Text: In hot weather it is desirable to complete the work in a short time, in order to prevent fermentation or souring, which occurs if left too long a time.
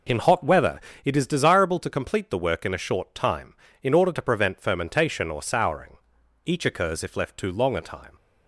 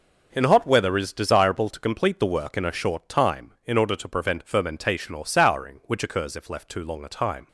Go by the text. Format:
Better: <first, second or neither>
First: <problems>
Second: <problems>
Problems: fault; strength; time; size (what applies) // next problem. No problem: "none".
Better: second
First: pauses between "weather" and "it"; slight; at 0.7 s; 0.24 s long // says "each" for "which"; at 6.4 s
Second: none